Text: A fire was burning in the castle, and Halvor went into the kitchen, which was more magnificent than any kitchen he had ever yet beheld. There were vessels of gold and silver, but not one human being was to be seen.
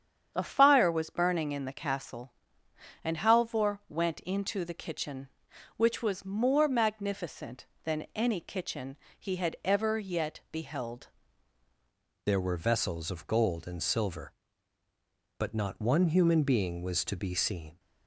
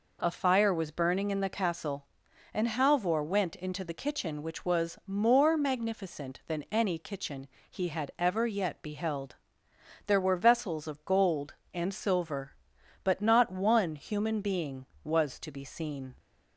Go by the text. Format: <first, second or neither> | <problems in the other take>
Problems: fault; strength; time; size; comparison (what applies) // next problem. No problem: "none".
second | starts louder than the rest; strong; until 1.3 s; 8 dB // pauses between "kitchen" and "he"; slight; at 8.9 s; 0.22 s long; slight in the second // changes voice at "There"; from 12.2 s on; 5.5 s long